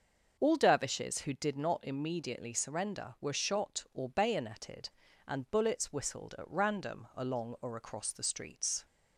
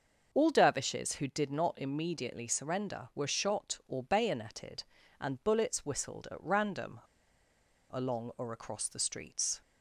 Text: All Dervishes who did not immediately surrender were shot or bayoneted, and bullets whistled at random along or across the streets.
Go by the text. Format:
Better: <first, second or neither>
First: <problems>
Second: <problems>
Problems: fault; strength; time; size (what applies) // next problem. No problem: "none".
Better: first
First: starts louder than the rest; until 1.4 s; 6.5 dB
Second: starts louder than the rest; until 1.3 s; 6.5 dB // pauses between "random" and "along"; noticeable; at 6.9 s; 0.93 s long